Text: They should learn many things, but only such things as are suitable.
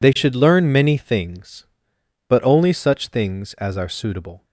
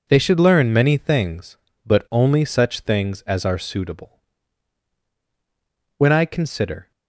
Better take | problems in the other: first | goes on to say "When I consider"; noticeable; from 5.9 s on; 0.94 s long

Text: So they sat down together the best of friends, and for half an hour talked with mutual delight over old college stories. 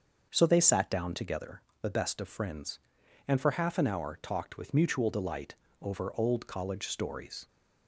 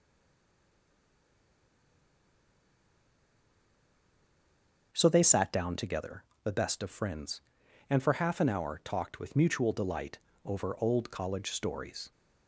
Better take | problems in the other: first | stays silent before the first word; strong; until 4.9 s; 4.9 s long // starts louder than the rest; until 5.9 s; 6.5 dB; also in the first // pauses between "together" and "the"; slight; at 6.2 s; 0.20 s long; slight in the first // pauses between "delight" and "over"; slight; at 10.1 s; 0.26 s long; slight in the first

